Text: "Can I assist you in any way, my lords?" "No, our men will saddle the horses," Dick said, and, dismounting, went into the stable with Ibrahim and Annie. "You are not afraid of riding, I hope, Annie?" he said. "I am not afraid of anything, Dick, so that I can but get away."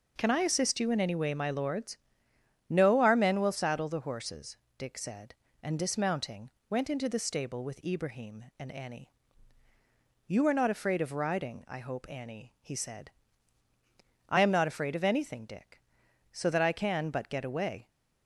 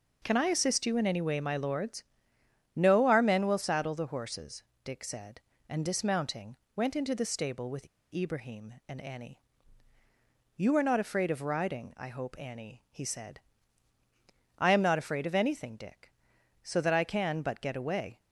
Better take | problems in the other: first | pauses between "with" and "Ibrahim"; slight; at 7.8 s; 0.25 s long

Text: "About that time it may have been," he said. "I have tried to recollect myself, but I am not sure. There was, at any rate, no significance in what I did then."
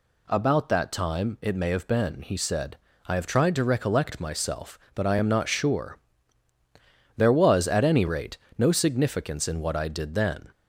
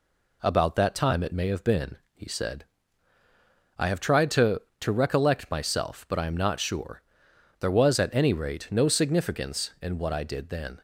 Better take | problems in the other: first | says "to" twice; at 4.7 s

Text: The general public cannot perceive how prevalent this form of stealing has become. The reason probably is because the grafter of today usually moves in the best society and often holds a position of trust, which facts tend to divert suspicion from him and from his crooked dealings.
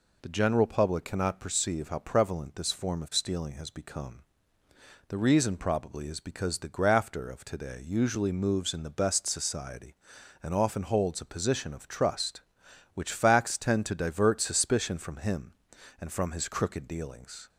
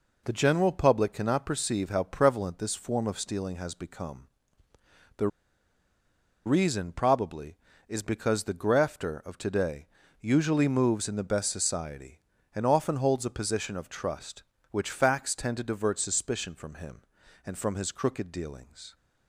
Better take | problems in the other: first | pauses between "The" and "reason"; at 5.2 s; 1.1 s long // pauses between "today" and "usually"; slight; at 9.8 s; 0.32 s long

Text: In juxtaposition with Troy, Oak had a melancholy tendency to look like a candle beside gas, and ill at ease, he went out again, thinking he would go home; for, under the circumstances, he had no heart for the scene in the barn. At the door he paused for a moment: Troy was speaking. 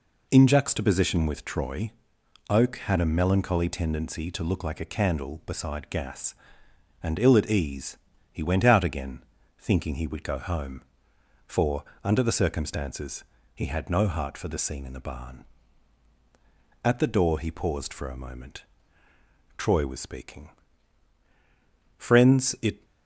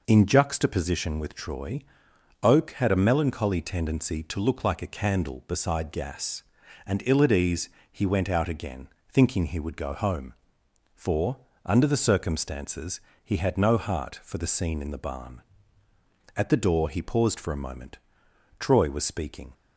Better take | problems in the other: second | goes on to say "Friends it"; noticeable; from 21.9 s on; 0.86 s long

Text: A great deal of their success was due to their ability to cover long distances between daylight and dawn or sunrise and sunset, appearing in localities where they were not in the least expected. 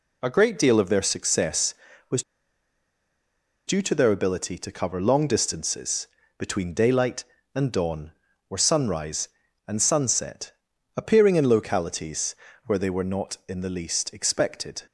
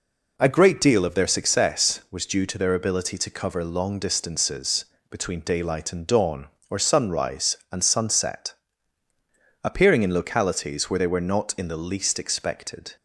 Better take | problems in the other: second | pauses between "was" and "due"; strong; at 2.2 s; 1.4 s long // pauses between "distances" and "between"; slight; at 6.0 s; 0.30 s long; slight in the second // pauses between "localities" and "where"; slight; at 12.3 s; 0.32 s long

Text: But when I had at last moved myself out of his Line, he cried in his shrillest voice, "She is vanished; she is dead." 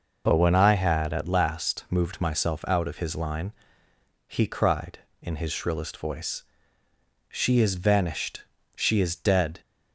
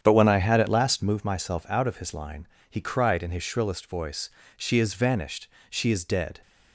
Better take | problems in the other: first | starts louder than the rest; strong; until 1.2 s; 8.5 dB

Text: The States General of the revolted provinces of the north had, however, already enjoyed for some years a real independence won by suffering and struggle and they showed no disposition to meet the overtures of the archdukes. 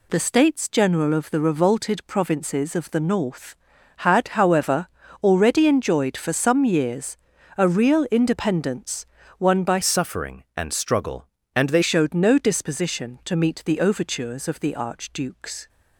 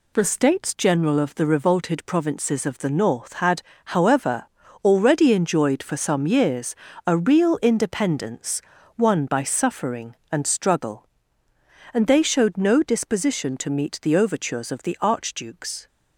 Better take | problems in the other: second | pauses between "years" and "a"; at 7.1 s; 0.40 s long; slight in the second // pauses between "independence" and "won"; slight; at 9.0 s; 0.34 s long; slight in the second // changes voice from "suffering" to "they"; from 9.8 to 11.8 s; 2.0 s long

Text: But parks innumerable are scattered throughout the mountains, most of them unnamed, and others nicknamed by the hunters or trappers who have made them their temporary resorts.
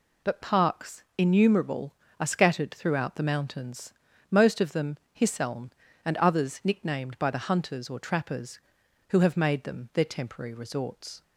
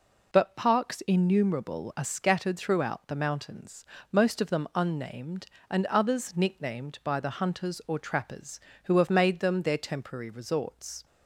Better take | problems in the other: second | says "hisseln" for "unnamed"; at 5.1 s

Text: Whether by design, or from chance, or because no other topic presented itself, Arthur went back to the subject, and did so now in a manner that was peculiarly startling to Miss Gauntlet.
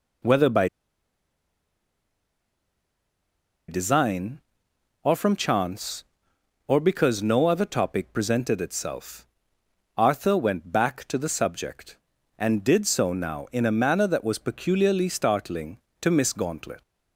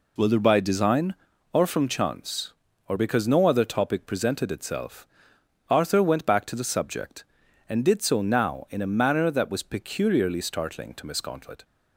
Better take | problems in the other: second | pauses between "by" and "design"; strong; at 0.6 s; 3.0 s long

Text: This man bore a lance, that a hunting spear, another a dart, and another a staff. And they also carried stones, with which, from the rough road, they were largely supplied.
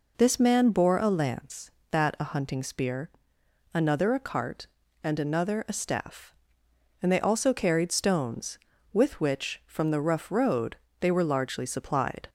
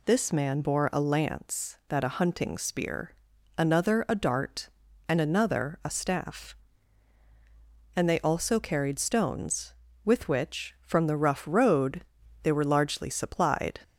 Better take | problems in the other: second | says "cart" for "dart"; at 4.1 s

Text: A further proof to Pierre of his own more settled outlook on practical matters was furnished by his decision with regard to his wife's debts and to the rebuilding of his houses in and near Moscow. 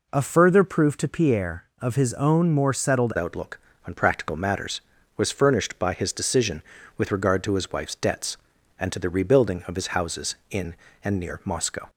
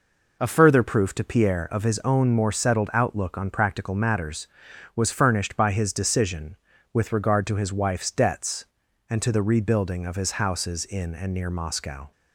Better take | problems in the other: second | changes voice at "outlook"; from 3.1 s on; 8.7 s long

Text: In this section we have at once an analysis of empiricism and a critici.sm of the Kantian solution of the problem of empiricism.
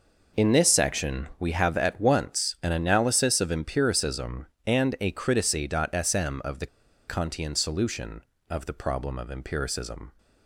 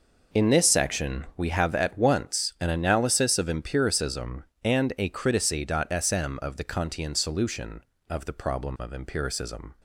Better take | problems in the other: second | pauses between "the" and "Kantian"; at 6.6 s; 0.40 s long

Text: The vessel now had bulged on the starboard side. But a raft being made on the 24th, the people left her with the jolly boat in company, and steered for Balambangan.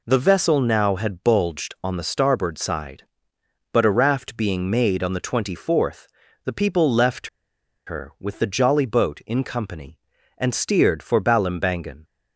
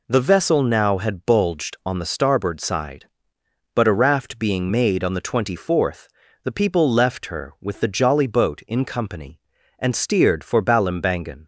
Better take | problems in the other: second | pauses between "left" and "her"; noticeable; at 7.2 s; 0.58 s long

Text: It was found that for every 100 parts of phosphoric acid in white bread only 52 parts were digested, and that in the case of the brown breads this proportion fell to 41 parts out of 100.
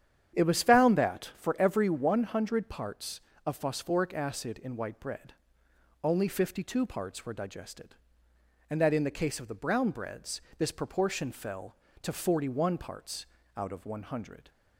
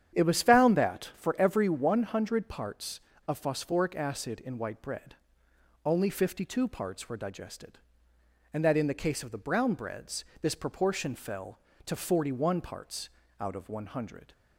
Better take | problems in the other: neither | starts louder than the rest; strong; the same in both // pauses between "bread" and "only"; noticeable; the same in both // pauses between "breads" and "this"; slight; the same in both // pauses between "parts" and "out"; slight; the same in both

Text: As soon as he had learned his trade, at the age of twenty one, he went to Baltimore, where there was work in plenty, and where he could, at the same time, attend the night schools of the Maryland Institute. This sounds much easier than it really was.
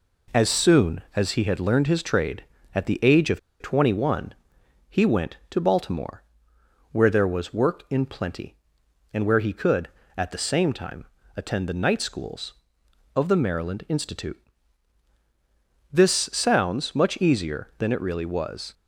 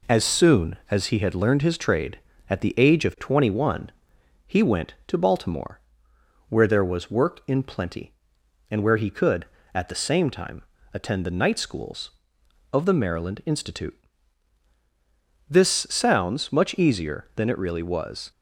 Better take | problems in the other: second | pauses between "of" and "twenty"; slight; at 3.3 s; 0.21 s long

